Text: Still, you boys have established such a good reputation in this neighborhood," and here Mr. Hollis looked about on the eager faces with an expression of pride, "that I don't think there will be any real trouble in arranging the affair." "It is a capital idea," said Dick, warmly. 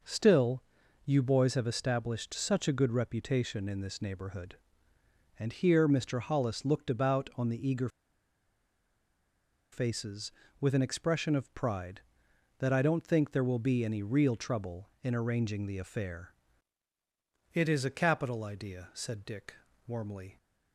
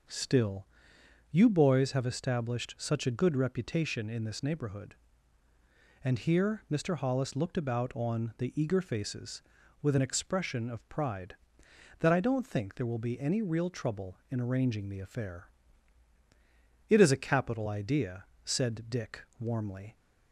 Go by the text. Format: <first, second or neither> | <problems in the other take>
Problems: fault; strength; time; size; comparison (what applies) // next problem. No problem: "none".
second | pauses between "eager" and "faces"; strong; at 7.8 s; 1.8 s long